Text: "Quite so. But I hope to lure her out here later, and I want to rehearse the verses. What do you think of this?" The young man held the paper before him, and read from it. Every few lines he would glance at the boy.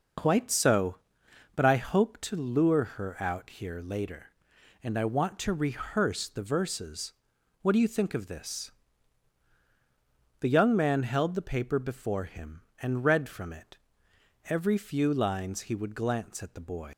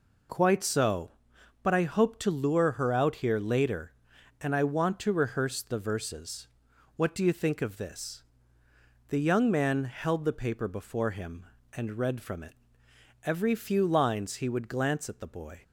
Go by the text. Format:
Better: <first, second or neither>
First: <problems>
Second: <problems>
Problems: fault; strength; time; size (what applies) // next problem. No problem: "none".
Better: second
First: leaves "boy" unfinished; at 16.9 s; 115 ms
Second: none